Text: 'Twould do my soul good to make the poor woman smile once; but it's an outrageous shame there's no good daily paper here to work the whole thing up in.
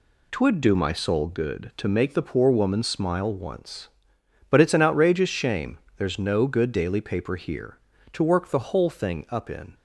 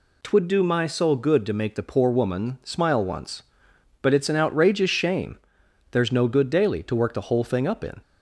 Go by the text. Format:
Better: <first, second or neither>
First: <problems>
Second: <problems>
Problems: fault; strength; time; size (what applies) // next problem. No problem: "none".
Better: first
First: pauses between "shame" and "there's"; slight; at 5.7 s; 0.20 s long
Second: pauses between "shame" and "there's"; noticeable; at 5.3 s; 0.52 s long // skips "paper here"; at 6.8 s